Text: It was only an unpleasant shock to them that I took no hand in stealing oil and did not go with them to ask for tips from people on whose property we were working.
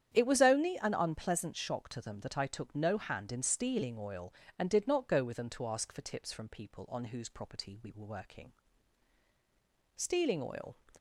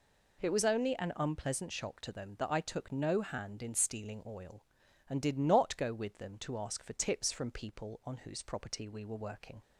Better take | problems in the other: second | starts louder than the rest; strong; until 1.1 s; 9.5 dB // goes on to say "Stealing oil"; noticeable; from 9.9 s on; 0.78 s long

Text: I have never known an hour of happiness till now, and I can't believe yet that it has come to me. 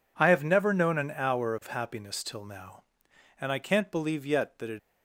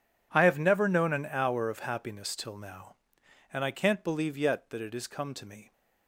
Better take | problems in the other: second | stops before "has come to me"; at 4.7 s

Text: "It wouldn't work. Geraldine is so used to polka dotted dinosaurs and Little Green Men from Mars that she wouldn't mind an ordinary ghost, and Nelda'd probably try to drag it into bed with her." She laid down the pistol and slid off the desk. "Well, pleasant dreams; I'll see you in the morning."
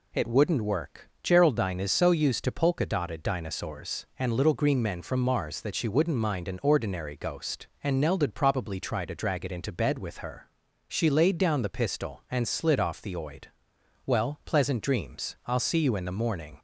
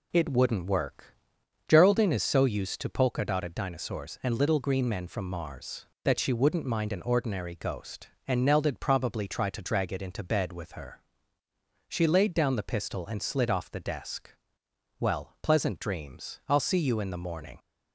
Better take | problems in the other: second | says "oid" for "desk"; at 13.1 s

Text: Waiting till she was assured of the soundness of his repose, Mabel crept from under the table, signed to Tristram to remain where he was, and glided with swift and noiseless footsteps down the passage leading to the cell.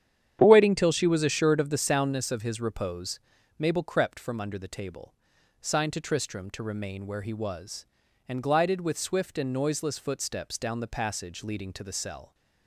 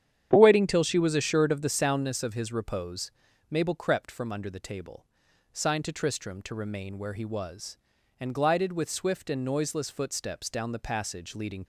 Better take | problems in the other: first | starts louder than the rest; strong; until 1.4 s; 9 dB; strong in the first // stops before "to the cell"; at 11.6 s

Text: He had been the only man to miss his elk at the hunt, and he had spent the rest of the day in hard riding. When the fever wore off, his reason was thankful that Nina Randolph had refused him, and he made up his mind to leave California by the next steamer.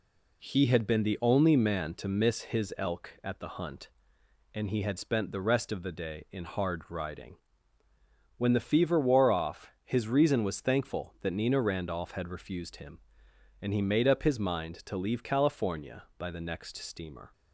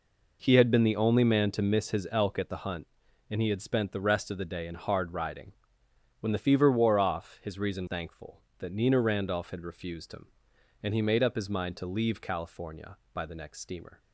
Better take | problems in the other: first | skips "was"; at 7.8 s

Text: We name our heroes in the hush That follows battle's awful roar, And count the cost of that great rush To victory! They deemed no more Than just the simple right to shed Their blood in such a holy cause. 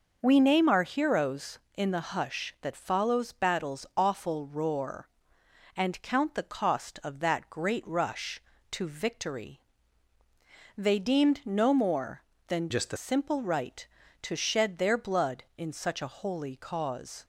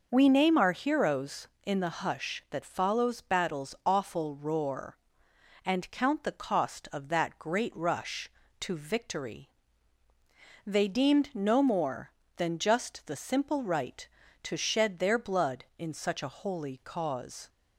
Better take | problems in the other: second | changes voice from "just" to "the"; from 12.7 to 12.9 s; 0.2 s long

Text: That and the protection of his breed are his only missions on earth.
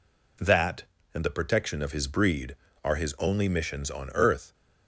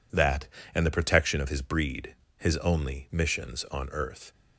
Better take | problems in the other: first | skips "are"; at 2.2 s

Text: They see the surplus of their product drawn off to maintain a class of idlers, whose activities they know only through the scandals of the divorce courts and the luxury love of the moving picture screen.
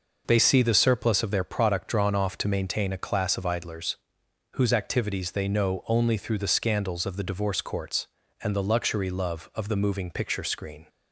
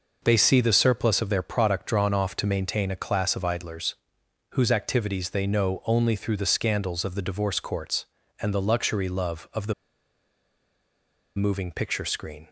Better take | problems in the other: first | pauses between "the" and "moving"; strong; at 9.7 s; 1.6 s long

